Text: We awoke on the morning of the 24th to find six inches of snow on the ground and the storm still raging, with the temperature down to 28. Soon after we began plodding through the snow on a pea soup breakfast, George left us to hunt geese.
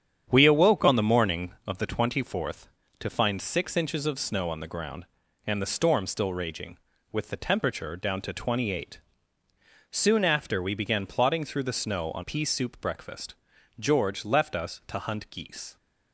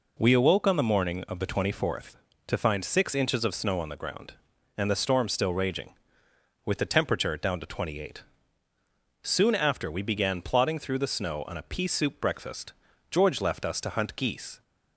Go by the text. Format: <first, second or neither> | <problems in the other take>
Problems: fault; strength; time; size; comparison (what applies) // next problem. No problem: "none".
second | starts louder than the rest; strong; until 1.3 s; 8.5 dB // skips "a"; at 12.2 s